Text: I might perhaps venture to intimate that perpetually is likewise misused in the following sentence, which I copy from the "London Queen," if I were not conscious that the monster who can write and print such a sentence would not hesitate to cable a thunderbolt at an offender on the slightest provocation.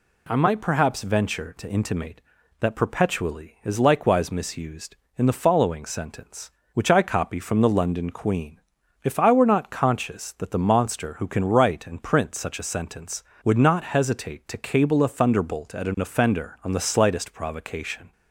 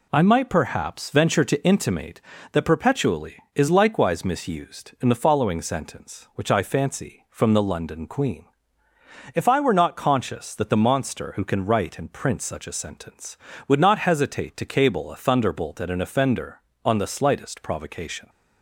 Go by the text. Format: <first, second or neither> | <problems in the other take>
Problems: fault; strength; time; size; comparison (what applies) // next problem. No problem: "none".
first | says "fancy" for "copy"; at 6.6 s